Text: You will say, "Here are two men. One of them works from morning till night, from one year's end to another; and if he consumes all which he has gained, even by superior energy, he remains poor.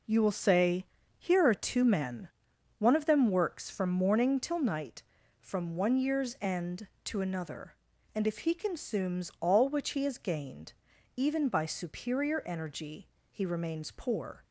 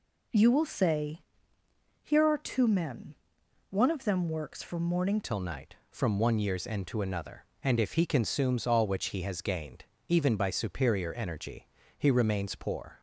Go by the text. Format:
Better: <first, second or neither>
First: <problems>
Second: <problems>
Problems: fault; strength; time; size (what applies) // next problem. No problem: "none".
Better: first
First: none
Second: changes voice at "till"; from 5.2 s on; 7.7 s long